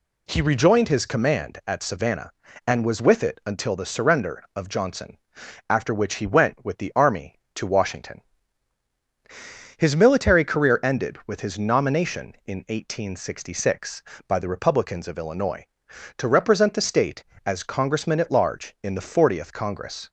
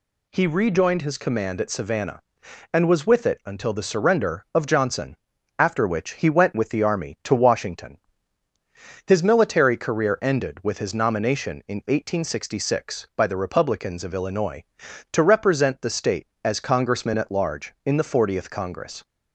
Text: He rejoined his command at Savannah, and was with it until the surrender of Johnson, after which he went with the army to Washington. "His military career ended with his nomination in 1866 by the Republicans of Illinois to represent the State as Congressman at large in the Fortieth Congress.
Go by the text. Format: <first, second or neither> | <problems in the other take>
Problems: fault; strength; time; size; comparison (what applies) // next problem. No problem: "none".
neither | none